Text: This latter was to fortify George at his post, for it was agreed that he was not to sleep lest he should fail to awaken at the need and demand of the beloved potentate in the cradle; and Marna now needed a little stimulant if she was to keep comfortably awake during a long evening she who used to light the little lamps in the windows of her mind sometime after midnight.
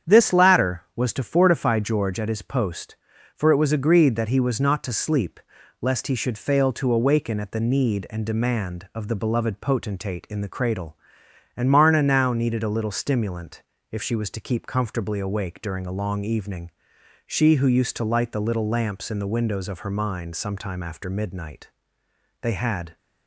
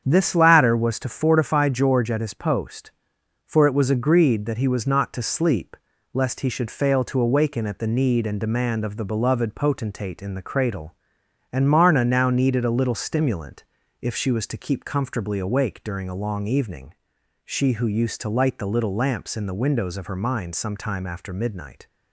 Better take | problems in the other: second | starts louder than the rest; strong; until 1.2 s; 8.5 dB; strong in the second // pauses between "sleep" and "lest"; at 5.4 s; 0.40 s long; also in the second // pauses between "stimulant" and "if"; slight; at 13.6 s; 0.28 s long; also in the second // pauses between "evening" and "she"; noticeable; at 16.7 s; 0.56 s long; noticeable in the second // goes on to say "They had"; from 22.4 s on; 0.56 s long

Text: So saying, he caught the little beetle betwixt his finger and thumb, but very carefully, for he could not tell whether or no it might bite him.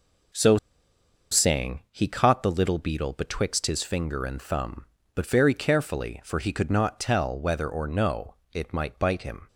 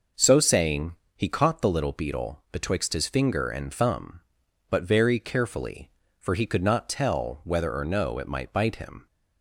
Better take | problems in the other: second | pauses between "So" and "saying"; noticeable; at 0.5 s; 0.74 s long // pauses between "no" and "it"; slight; at 8.3 s; 0.20 s long

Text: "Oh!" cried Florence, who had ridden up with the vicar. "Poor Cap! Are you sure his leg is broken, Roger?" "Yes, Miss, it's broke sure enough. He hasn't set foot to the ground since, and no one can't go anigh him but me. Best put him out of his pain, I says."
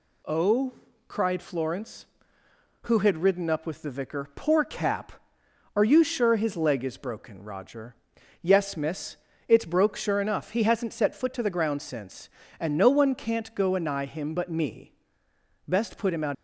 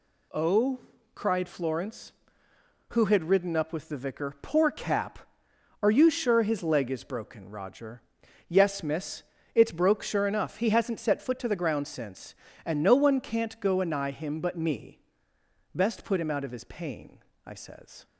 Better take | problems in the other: second | stops before "of his pain I says"; at 16.3 s

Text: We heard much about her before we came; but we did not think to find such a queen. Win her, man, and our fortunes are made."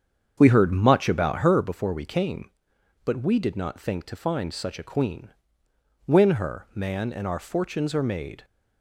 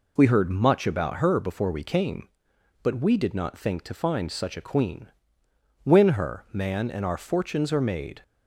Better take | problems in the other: second | starts louder than the rest; strong; until 1.7 s; 7.5 dB

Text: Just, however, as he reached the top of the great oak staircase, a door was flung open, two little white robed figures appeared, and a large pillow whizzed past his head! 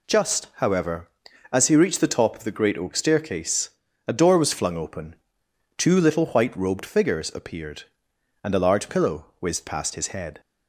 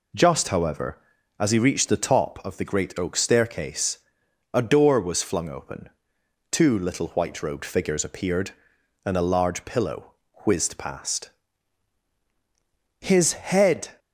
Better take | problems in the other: first | starts louder than the rest; slight; until 1.3 s; 3 dB // pauses between "pillow" and "whizzed"; slight; at 10.1 s; 0.32 s long // pauses between "past" and "his"; strong; at 11.3 s; 1.7 s long

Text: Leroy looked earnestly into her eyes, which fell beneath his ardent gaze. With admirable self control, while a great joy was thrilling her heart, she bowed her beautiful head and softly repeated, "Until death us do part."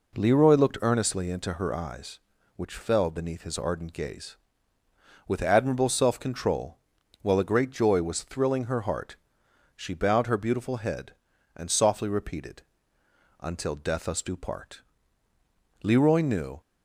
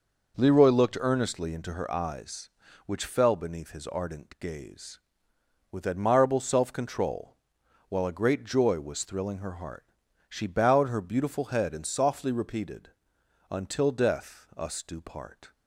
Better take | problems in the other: second | goes on to say "Leroy knew"; noticeable; from 15.8 s on; 0.78 s long

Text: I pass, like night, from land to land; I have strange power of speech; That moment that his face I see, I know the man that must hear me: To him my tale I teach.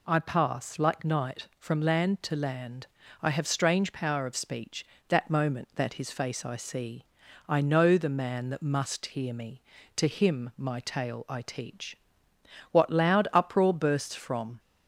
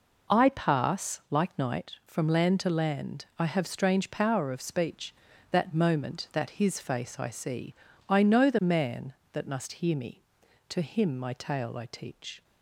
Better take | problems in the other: second | goes on to say "What loud uproar bursts from"; strong; from 12.7 s on; 1.8 s long

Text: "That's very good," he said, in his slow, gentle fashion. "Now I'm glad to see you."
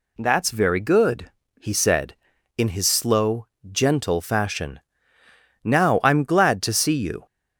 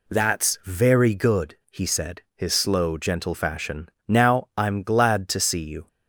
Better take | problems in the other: first | skips "in"; at 2.2 s

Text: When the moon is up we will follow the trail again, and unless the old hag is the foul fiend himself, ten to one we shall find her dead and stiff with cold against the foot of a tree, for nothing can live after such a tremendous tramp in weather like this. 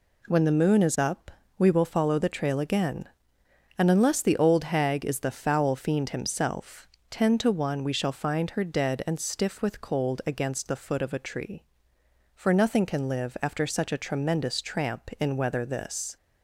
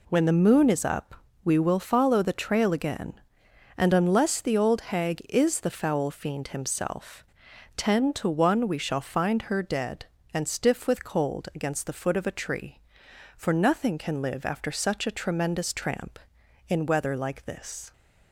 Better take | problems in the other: second | pauses between "up" and "we"; slight; at 1.3 s; 0.28 s long; slight in the second // skips "like"; at 15.6 s

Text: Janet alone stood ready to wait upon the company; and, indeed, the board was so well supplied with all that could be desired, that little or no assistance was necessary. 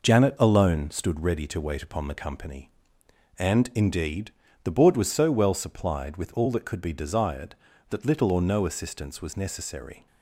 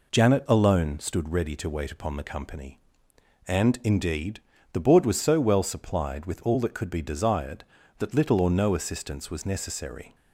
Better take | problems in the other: second | gets quieter; noticeable; throughout; 5 dB

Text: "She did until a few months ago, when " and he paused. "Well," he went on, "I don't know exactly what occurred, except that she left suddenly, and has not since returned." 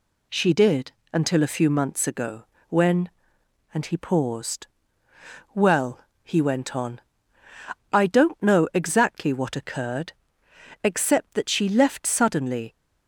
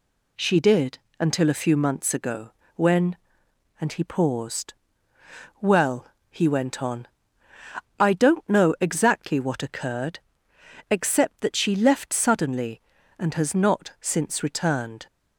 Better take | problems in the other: second | pauses between "did" and "until"; slight; at 0.9 s; 0.20 s long; slight in the second // stops before "and has not since returned"; at 12.7 s

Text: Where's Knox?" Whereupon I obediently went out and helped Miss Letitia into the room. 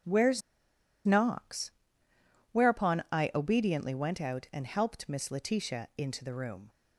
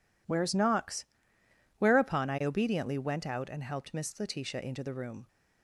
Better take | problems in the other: second | pauses between "Where's" and "Knox"; noticeable; at 0.4 s; 0.64 s long

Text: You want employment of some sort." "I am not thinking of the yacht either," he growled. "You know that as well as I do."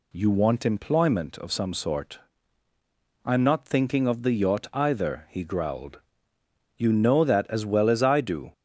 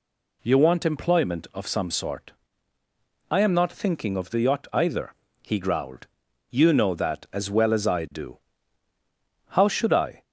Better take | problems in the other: first | goes on to say "How should I"; noticeable; from 9.5 s on; 0.72 s long

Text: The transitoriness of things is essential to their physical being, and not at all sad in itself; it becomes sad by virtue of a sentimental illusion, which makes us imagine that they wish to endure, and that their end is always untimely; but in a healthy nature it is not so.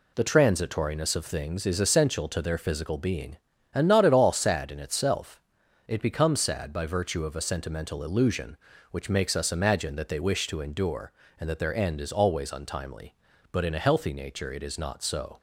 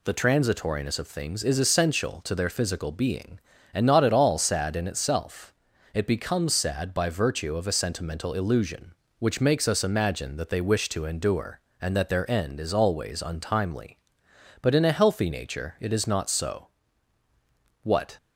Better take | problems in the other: first | goes on to say "What"; slight; from 17.8 s on; 0.34 s long

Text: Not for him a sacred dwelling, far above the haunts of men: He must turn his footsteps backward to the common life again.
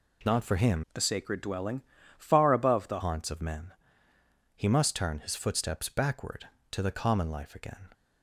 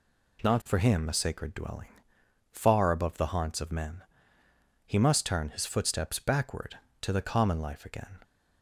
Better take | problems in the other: second | changes voice from "a" to "the"; from 0.9 to 2.9 s; 2.0 s long

